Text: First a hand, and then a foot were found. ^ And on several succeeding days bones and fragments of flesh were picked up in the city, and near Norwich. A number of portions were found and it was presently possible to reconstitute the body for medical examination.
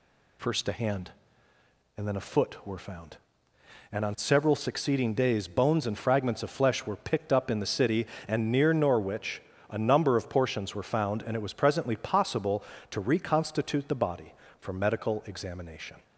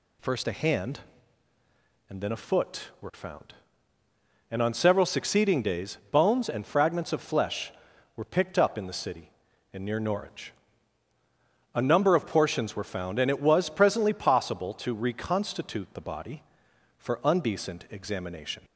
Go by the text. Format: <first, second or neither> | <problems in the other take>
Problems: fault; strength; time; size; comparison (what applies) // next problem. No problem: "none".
first | says "undecent" for "medical"; at 17.2 s